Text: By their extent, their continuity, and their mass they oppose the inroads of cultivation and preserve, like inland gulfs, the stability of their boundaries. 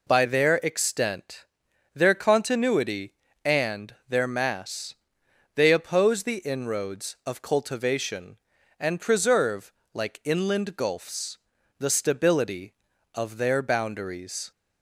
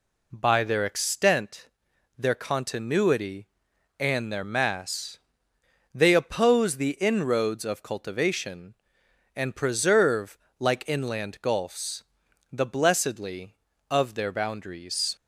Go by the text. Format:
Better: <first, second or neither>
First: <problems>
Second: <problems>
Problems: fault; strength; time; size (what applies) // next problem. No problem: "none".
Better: first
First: pauses between "mass" and "they"; noticeable; at 4.9 s; 0.60 s long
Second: pauses between "mass" and "they"; noticeable; at 5.1 s; 0.74 s long // says "blessedly" for "stability"; at 12.6 s